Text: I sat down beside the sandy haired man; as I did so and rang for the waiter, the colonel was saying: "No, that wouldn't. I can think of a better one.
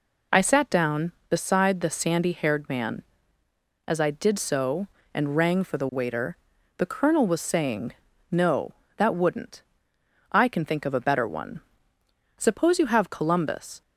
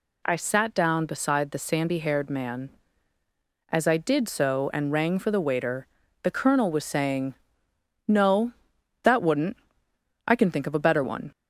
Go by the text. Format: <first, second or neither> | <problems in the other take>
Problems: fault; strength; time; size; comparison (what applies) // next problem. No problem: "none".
second | goes on to say "Suppose you have Columbus"; from 12.3 s on; 1.4 s long